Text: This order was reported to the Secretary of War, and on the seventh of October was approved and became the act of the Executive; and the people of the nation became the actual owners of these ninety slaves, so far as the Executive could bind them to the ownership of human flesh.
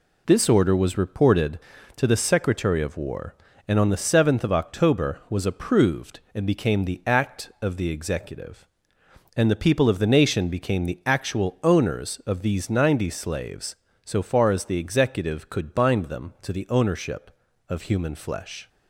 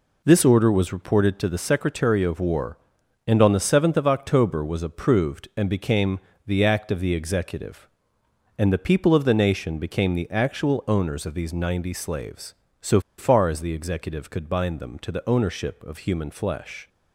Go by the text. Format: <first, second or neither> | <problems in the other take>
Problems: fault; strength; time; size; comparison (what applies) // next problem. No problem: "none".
first | pauses between "became" and "the"; slight; at 6.2 s; 0.26 s long // pauses between "so" and "far"; slight; at 13.0 s; 0.17 s long